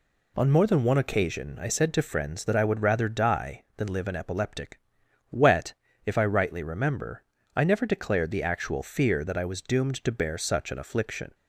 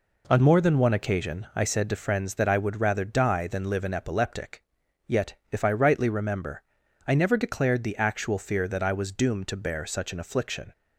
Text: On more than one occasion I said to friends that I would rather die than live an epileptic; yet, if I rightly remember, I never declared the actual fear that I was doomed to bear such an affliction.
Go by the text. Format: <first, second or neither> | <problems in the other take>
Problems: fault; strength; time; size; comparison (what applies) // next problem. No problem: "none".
second | says "wet" for "yet"; at 5.3 s